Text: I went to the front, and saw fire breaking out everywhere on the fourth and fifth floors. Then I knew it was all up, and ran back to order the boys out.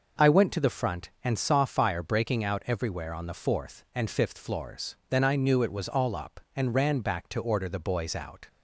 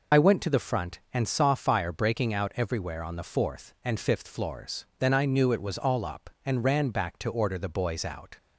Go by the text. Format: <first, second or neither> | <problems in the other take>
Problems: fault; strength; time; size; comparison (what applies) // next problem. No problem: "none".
first | loses the start of "I"; at 0.1 s; 50 ms